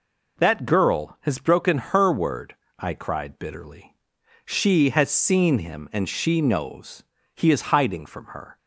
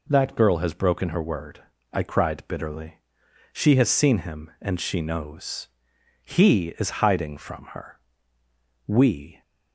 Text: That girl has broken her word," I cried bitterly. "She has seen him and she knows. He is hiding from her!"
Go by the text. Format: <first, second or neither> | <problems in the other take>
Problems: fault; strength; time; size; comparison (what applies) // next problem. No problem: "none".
first | goes on to say "We"; from 8.8 s on; 0.54 s long